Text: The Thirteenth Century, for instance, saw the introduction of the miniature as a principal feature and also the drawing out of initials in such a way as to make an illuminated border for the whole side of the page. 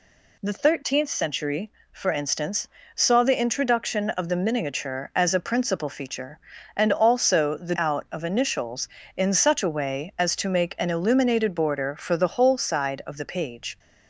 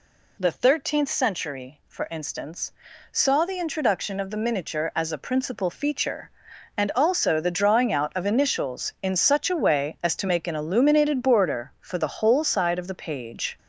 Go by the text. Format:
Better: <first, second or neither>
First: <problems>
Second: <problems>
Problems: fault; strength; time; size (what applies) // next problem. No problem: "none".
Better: second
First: skips "drawing"; at 7.7 s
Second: none